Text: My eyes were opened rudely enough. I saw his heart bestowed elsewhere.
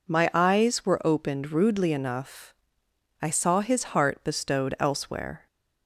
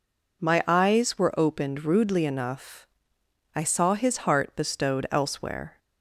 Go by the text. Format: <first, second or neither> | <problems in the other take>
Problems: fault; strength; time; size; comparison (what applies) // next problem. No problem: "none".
neither | none